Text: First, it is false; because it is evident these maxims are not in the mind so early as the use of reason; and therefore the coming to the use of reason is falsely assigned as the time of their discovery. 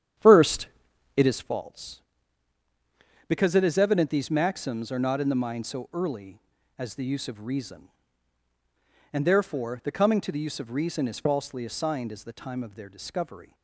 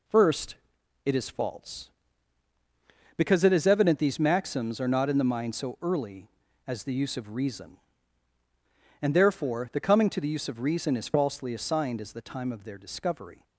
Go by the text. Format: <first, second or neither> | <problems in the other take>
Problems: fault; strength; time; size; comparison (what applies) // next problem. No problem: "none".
second | starts louder than the rest; strong; until 1.5 s; 9.5 dB